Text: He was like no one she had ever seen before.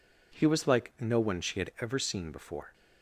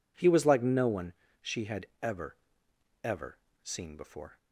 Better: first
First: none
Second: pauses between "one" and "she"; slight; at 1.1 s; 0.28 s long // says "ever" twice; at 3.0 s

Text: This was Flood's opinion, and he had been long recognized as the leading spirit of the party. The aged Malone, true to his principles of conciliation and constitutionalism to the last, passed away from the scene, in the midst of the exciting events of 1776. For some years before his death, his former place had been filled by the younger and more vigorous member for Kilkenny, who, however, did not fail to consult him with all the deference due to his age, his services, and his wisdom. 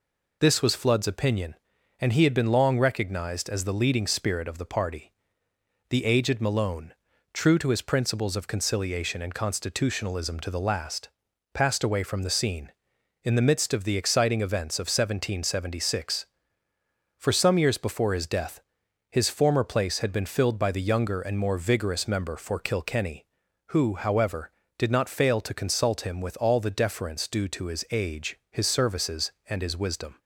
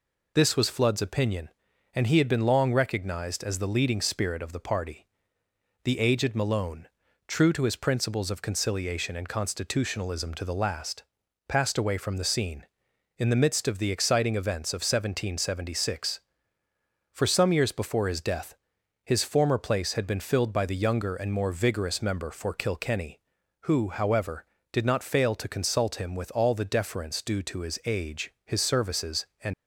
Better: first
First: none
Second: stops before "his wisdom"; at 29.5 s

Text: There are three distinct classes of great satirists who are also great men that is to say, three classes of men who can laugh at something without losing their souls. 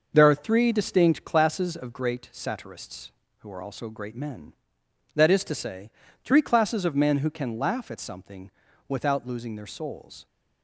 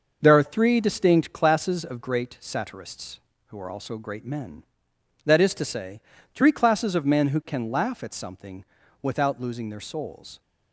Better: neither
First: starts louder than the rest; noticeable; until 1.1 s; 6 dB // pauses between "something" and "without"; at 8.4 s; 0.38 s long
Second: starts louder than the rest; noticeable; until 1.2 s; 6 dB // pauses between "something" and "without"; at 8.6 s; 0.38 s long

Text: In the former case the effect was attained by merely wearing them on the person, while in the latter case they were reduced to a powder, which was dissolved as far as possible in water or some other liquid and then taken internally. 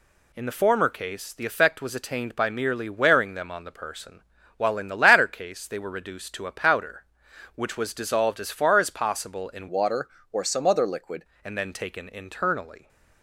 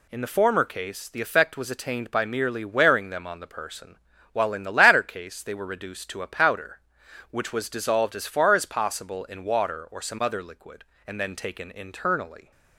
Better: second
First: changes voice from "water" to "liquid"; from 9.6 to 11.2 s; 1.6 s long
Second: none

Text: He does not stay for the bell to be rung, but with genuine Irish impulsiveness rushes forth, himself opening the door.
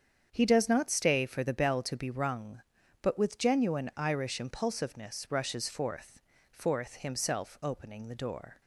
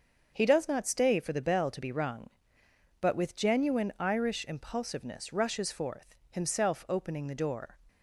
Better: second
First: starts louder than the rest; strong; until 1.3 s; 7.5 dB // says "forth" twice; at 6.5 s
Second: starts louder than the rest; until 1.3 s; 6.5 dB

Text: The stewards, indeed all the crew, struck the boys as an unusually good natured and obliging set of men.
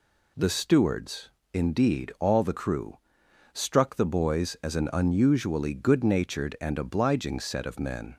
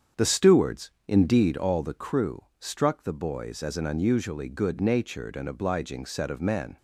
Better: first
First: none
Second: starts louder than the rest; strong; until 1.7 s; 7.5 dB

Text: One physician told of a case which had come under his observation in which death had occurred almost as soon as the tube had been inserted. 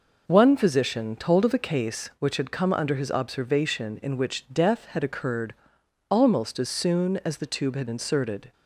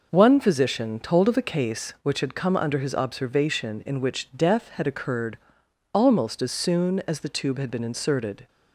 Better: second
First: pauses between "occurred" and "almost"; noticeable; at 5.5 s; 0.56 s long // skips "been"; at 7.8 s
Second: pauses between "occurred" and "almost"; noticeable; at 5.3 s; 0.56 s long

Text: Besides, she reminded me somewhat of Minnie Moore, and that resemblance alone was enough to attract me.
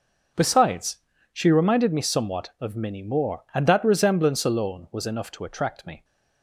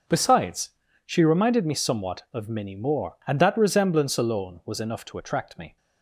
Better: neither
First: none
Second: none

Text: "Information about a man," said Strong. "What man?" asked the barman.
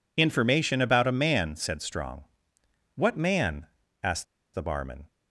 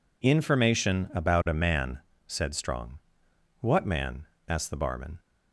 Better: second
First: pauses between "asked" and "the"; slight; at 4.2 s; 0.29 s long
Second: none

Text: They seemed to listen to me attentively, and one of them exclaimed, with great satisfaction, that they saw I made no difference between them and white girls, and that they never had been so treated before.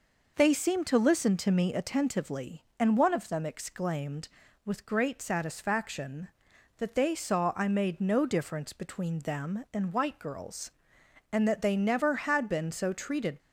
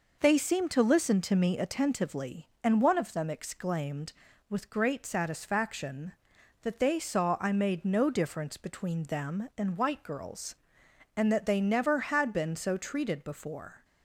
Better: second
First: stops before "before"; at 13.3 s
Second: none

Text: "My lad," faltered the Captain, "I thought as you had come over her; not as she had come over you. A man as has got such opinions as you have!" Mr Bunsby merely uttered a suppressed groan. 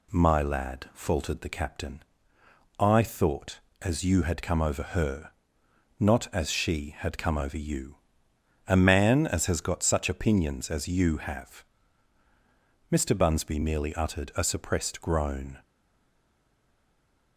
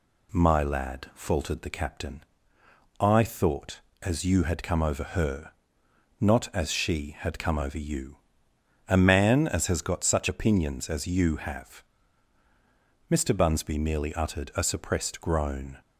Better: second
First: stays silent after the last word; noticeable; from 15.6 s on; 1.7 s long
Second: none

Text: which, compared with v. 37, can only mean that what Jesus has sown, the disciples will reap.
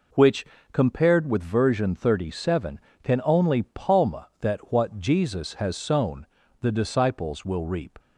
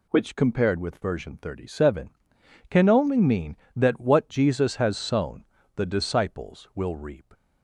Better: second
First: says "palma" for "mean"; at 3.6 s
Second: none

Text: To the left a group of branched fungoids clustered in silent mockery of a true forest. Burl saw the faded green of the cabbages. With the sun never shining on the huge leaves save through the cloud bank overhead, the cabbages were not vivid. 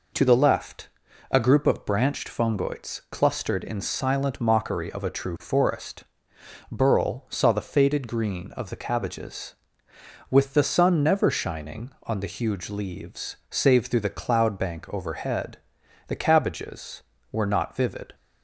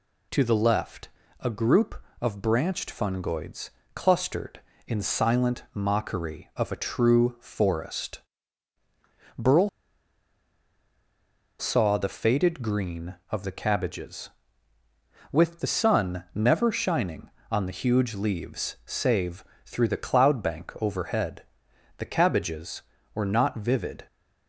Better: first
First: pauses between "left" and "a"; at 0.8 s; 0.42 s long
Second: pauses between "left" and "a"; slight; at 1.0 s; 0.32 s long // pauses between "fungoids" and "clustered"; slight; at 3.7 s; 0.24 s long // pauses between "Burl" and "saw"; strong; at 9.6 s; 1.9 s long // pauses between "save" and "through"; slight; at 19.4 s; 0.22 s long

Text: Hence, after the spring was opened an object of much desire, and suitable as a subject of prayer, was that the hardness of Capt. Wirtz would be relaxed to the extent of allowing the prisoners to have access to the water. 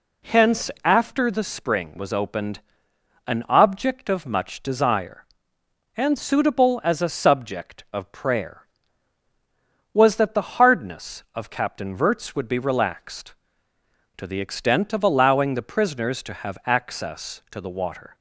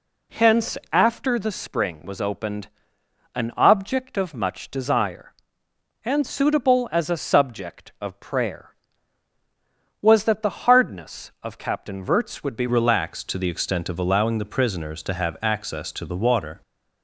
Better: first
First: pauses between "opened" and "an"; noticeable; at 2.6 s; 0.66 s long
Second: pauses between "opened" and "an"; noticeable; at 2.6 s; 0.66 s long // changes voice at "relaxed"; from 12.6 s on; 4.0 s long

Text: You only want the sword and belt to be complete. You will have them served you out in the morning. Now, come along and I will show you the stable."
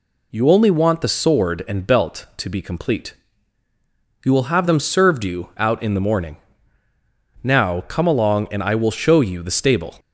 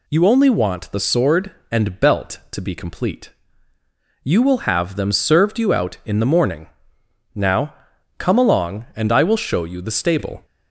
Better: neither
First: none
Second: none

